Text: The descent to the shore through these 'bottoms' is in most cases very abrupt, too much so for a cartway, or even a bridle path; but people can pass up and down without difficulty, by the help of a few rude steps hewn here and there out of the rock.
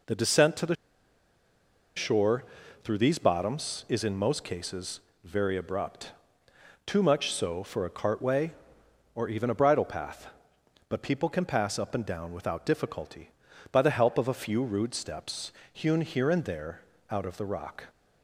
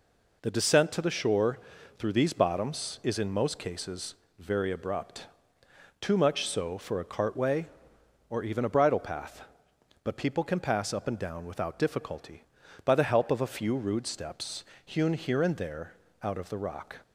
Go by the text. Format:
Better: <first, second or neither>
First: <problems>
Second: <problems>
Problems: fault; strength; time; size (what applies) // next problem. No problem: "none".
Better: second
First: pauses between "the" and "shore"; at 0.7 s; 1.2 s long // pauses between "shore" and "through"; at 2.4 s; 0.40 s long // pauses between "cases" and "very"; slight; at 4.9 s; 0.24 s long // pauses between "steps" and "hewn"; slight; at 15.5 s; 0.20 s long // pauses between "there" and "out"; slight; at 16.8 s; 0.28 s long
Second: pauses between "shore" and "through"; at 1.5 s; 0.40 s long // pauses between "cases" and "very"; slight; at 4.1 s; 0.24 s long // pauses between "steps" and "hewn"; slight; at 14.6 s; 0.20 s long // pauses between "there" and "out"; slight; at 15.9 s; 0.28 s long